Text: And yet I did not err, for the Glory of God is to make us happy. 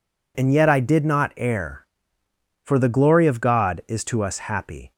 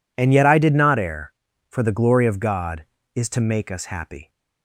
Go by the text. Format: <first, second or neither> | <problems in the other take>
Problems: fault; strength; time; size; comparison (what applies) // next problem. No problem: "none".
second | skips "make"; at 4.2 s